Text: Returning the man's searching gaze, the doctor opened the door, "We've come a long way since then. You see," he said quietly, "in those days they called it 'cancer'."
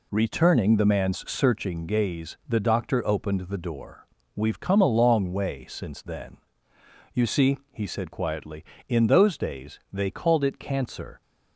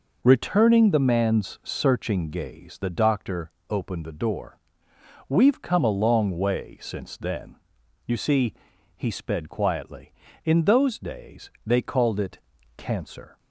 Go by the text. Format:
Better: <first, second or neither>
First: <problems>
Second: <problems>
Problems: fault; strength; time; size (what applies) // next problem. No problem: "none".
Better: first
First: none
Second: pauses between "doctor" and "opened"; slight; at 3.4 s; 0.22 s long // says "sped" for "said"; at 9.0 s // pauses between "days" and "they"; slight; at 11.4 s; 0.16 s long // pauses between "it" and "cancer"; at 12.3 s; 0.40 s long